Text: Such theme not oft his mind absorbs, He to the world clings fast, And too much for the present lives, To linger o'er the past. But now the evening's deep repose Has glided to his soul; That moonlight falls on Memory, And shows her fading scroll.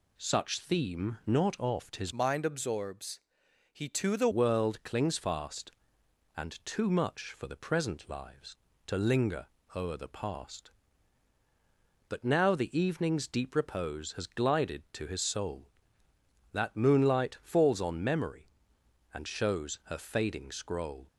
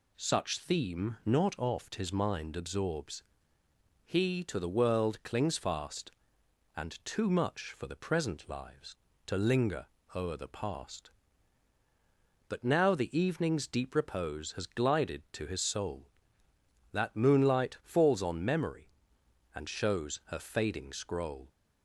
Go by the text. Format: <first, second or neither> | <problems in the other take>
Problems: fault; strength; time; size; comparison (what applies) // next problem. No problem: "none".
second | changes voice from "mind" to "the"; from 2.1 to 4.2 s; 2.1 s long // pauses between "linger" and "o'er"; slight; at 9.4 s; 0.28 s long; slight in the second